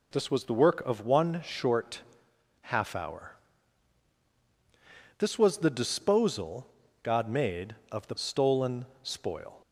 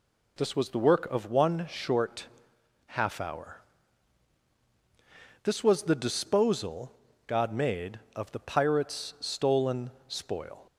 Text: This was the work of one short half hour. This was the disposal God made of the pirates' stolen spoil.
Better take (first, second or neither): second